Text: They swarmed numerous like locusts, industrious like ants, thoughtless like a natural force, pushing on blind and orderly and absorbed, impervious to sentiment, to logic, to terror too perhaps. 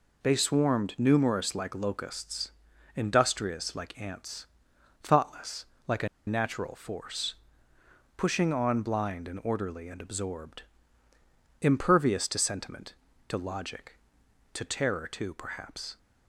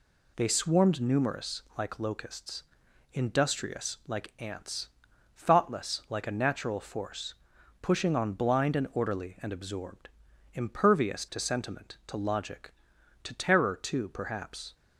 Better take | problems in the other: second | pauses between "thoughtless" and "like"; slight; at 5.6 s; 0.22 s long // pauses between "a" and "natural"; slight; at 6.0 s; 0.19 s long

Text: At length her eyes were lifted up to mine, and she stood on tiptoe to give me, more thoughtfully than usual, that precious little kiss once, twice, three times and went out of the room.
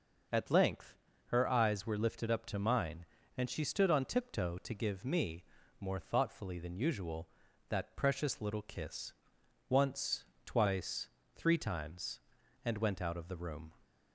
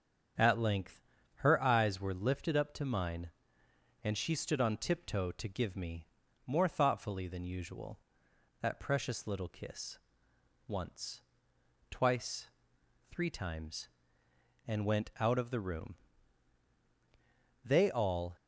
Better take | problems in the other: first | starts louder than the rest; strong; until 1.7 s; 7.5 dB // pauses between "length" and "her"; slight; at 1.0 s; 0.34 s long; slight in the first // pauses between "kiss" and "once"; noticeable; at 9.9 s; 0.70 s long; noticeable in the first // goes on to say "They all"; noticeable; from 17.6 s on; 0.72 s long

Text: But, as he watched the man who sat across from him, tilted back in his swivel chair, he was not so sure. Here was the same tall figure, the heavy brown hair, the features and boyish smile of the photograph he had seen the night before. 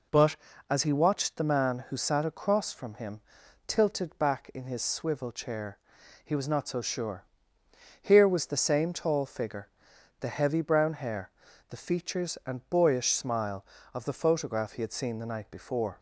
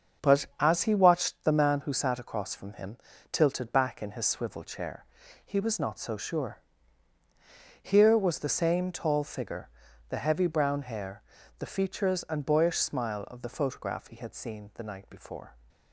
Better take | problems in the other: first | gets quieter; throughout; 6.5 dB

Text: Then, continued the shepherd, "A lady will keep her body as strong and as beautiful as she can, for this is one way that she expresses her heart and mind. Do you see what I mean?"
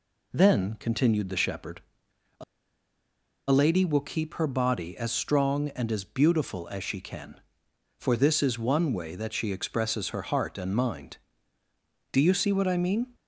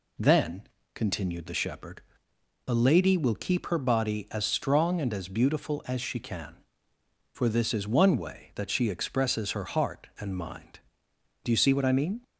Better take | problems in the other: second | pauses between "A" and "lady"; at 2.4 s; 1.0 s long

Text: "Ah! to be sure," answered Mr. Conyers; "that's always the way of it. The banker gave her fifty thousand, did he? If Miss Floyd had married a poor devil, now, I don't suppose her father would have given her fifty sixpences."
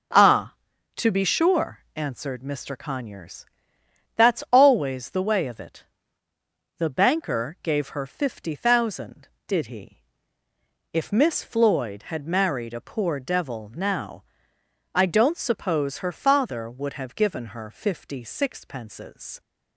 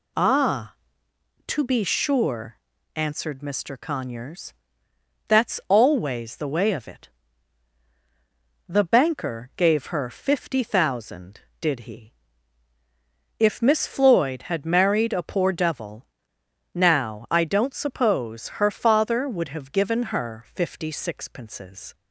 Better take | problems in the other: neither | none

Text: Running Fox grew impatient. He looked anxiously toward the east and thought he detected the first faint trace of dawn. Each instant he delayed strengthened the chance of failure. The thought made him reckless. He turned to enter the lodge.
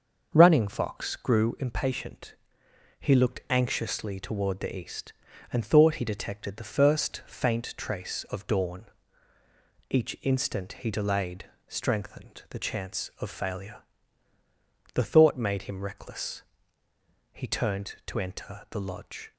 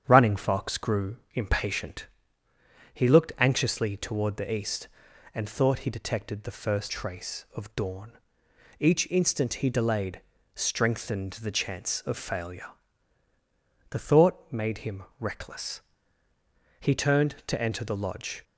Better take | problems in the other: first | starts louder than the rest; strong; until 1.0 s; 8.5 dB; noticeable in the first // pauses between "grew" and "impatient"; slight; at 1.1 s; 0.16 s long // skips "faint"; at 6.9 s // pauses between "delayed" and "strengthened"; slight; at 10.1 s; 0.34 s long; slight in the first // pauses between "him" and "reckless"; slight; at 15.0 s; 0.16 s long

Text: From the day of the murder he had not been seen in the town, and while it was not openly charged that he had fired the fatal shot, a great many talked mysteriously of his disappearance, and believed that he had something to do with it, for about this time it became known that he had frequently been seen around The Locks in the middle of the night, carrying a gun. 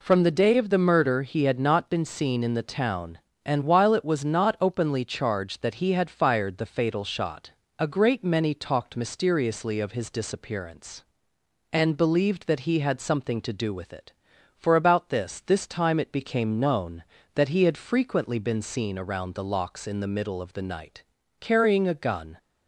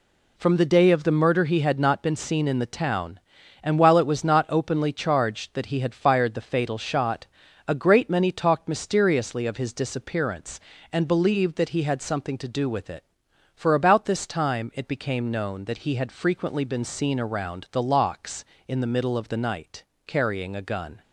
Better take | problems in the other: second | says "this" twice; at 15.4 s

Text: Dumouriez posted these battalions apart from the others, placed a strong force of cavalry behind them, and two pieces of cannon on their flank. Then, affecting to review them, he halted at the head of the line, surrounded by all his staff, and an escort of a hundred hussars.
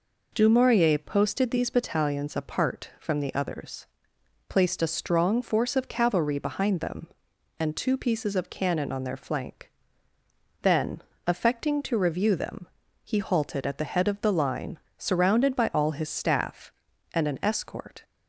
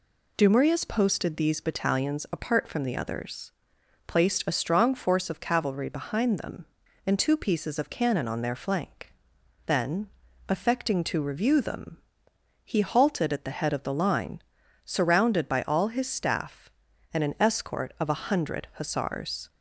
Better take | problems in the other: second | stops before "of a hundred hussars"; at 18.0 s

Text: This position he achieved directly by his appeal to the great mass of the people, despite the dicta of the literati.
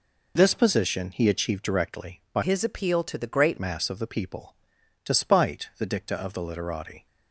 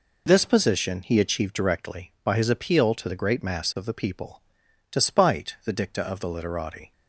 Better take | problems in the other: second | changes voice from "his" to "great"; from 2.4 to 3.5 s; 1.1 s long

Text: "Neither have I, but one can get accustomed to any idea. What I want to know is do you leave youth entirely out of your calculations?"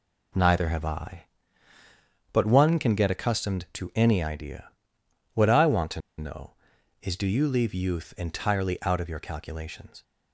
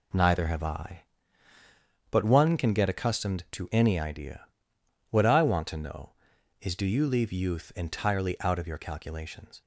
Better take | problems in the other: second | pauses between "to" and "know"; slight; at 5.9 s; 0.18 s long

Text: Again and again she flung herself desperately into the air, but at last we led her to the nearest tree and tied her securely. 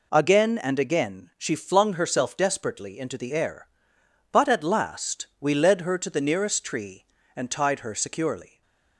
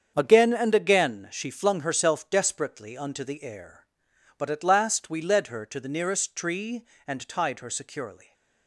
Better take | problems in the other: first | starts louder than the rest; strong; until 1.1 s; 7.5 dB // says "unto" for "into"; at 2.9 s // stays silent after the last word; slight; from 8.1 s on; 0.5 s long; slight in the first

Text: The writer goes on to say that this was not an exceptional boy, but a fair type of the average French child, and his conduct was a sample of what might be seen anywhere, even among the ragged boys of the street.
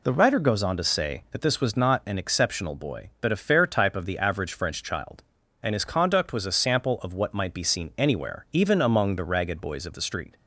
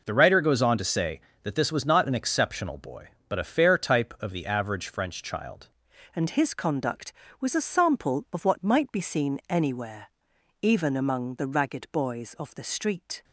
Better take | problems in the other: first | changes voice at "and"; from 6.1 s on; 7.1 s long

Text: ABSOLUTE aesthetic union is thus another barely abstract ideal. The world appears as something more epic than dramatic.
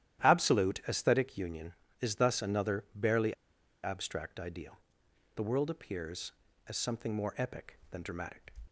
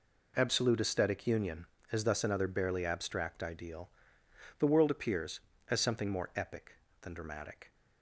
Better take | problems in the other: second | starts louder than the rest; strong; until 1.2 s; 12 dB // pauses between "barely" and "abstract"; noticeable; at 3.3 s; 0.49 s long

